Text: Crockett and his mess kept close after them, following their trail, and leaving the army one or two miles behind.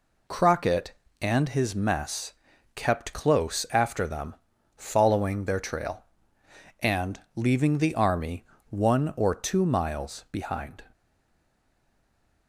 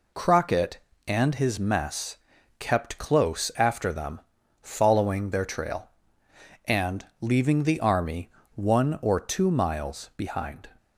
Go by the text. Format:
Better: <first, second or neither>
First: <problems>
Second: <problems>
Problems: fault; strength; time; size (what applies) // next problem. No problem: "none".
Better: second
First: pauses between "mess" and "kept"; at 2.3 s; 0.42 s long // pauses between "and" and "leaving"; slight; at 7.1 s; 0.16 s long // pauses between "army" and "one"; slight; at 8.4 s; 0.24 s long // stays silent after the last word; noticeable; from 10.9 s on; 1.5 s long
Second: pauses between "mess" and "kept"; at 2.1 s; 0.42 s long // pauses between "and" and "leaving"; slight; at 7.0 s; 0.16 s long // pauses between "army" and "one"; slight; at 8.3 s; 0.24 s long